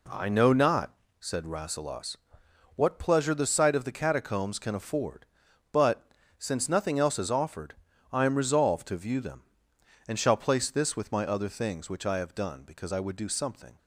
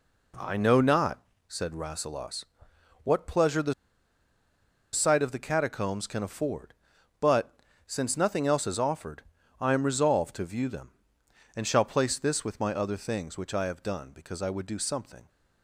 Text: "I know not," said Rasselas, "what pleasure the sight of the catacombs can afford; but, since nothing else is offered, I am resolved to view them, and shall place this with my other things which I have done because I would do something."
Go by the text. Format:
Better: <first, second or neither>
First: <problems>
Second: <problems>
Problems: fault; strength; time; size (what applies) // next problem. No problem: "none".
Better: first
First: none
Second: pauses between "the" and "sight"; at 3.7 s; 1.2 s long